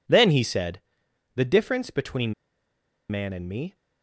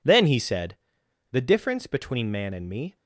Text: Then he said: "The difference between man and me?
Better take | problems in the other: second | pauses between "between" and "man"; noticeable; at 2.3 s; 0.76 s long

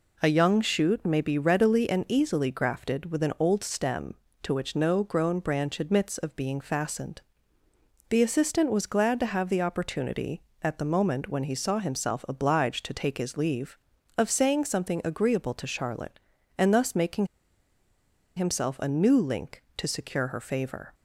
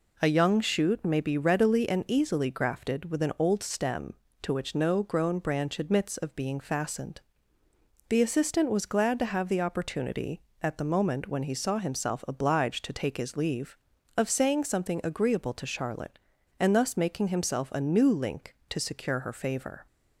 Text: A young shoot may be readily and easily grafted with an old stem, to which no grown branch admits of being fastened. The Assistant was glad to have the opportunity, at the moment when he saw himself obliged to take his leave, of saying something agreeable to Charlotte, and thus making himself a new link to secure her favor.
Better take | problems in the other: second | pauses between "making" and "himself"; at 17.2 s; 1.0 s long

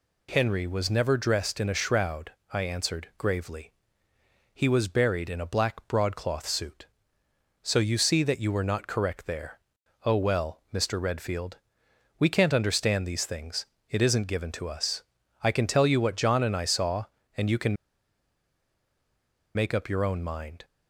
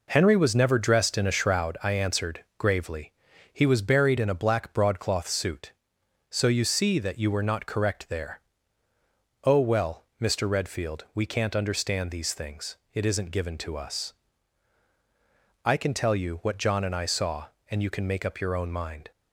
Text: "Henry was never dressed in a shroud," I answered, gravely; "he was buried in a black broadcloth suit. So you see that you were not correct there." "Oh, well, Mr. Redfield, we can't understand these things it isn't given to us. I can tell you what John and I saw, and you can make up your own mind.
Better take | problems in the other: second | pauses between "things" and "it"; slight; at 13.6 s; 0.24 s long; slight in the second // pauses between "can" and "make"; strong; at 17.7 s; 1.7 s long

